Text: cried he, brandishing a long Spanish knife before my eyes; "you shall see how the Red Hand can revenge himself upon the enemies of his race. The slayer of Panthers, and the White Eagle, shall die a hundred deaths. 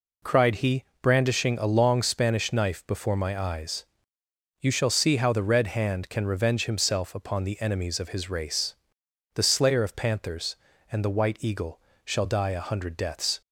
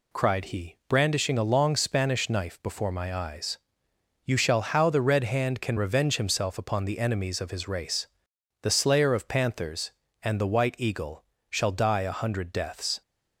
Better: first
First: none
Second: skips "see"; at 4.6 s

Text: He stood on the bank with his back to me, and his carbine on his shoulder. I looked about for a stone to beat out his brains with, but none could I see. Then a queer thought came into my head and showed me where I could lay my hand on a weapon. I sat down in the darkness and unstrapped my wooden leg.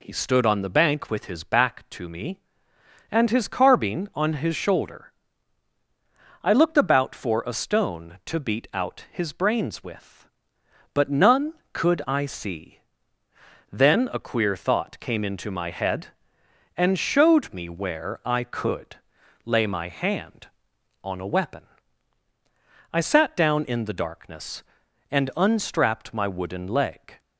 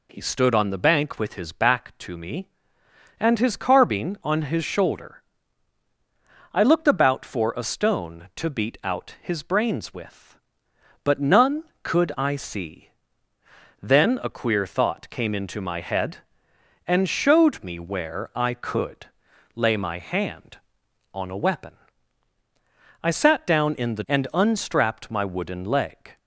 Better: first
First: pauses between "could" and "lay"; noticeable; at 18.9 s; 0.48 s long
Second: pauses between "could" and "lay"; noticeable; at 19.0 s; 0.48 s long // skips "darkness"; at 24.0 s

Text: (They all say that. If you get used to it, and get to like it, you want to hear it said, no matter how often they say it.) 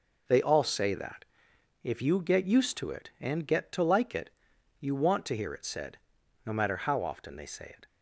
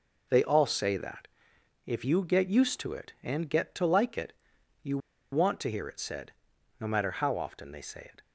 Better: first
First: none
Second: pauses between "you" and "want"; slight; at 4.9 s; 0.34 s long

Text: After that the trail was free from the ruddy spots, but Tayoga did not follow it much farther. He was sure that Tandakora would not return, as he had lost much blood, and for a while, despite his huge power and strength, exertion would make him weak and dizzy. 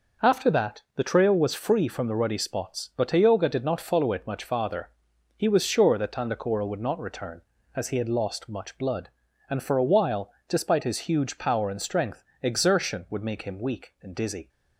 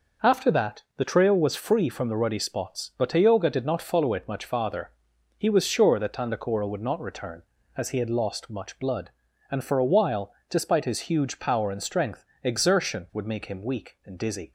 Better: neither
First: none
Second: none

